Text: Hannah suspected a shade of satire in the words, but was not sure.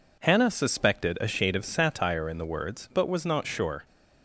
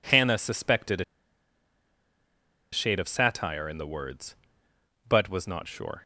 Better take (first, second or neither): first